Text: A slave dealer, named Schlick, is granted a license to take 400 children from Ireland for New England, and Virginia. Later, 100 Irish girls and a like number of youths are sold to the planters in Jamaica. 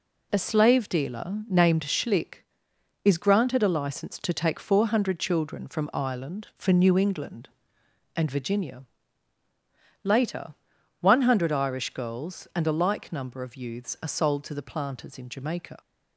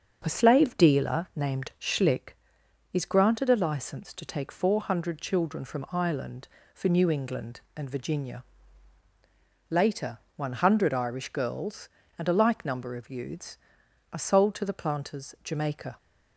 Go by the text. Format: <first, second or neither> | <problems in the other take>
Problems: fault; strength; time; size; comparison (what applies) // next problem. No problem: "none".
first | starts louder than the rest; until 1.2 s; 6.5 dB // skips "in"; at 15.3 s